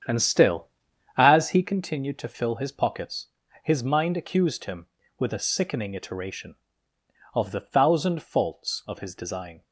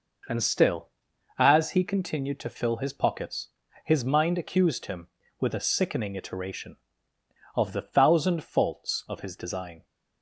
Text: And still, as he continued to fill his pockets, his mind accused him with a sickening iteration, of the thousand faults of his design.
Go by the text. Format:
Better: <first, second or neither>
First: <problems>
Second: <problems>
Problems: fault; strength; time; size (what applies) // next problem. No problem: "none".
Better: second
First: starts louder than the rest; strong; until 1.7 s; 8 dB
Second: none